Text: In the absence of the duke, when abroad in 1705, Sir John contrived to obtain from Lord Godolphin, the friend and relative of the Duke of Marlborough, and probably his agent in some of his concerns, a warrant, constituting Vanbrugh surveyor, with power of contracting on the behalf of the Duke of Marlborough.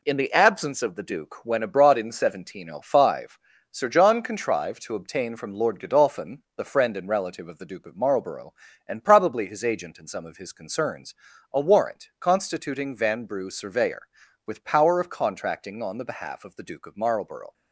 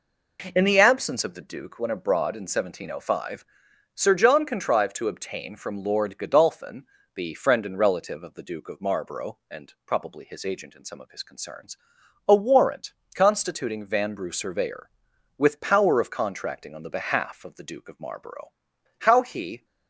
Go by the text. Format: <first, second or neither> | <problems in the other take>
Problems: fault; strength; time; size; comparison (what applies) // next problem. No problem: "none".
first | goes on to say "How he"; noticeable; from 18.9 s on; 0.66 s long